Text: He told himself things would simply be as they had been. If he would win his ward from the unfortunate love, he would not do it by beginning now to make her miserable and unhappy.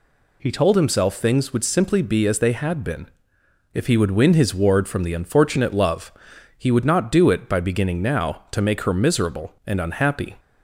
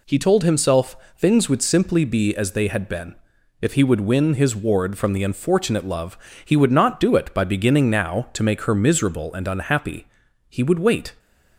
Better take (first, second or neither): first